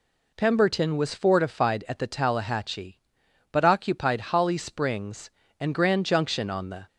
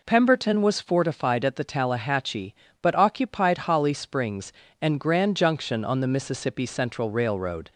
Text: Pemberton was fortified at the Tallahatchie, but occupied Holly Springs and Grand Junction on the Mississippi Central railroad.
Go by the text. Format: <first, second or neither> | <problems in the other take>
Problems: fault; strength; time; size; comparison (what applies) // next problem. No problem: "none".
second | stops before "Mississippi Central railroad"; at 6.8 s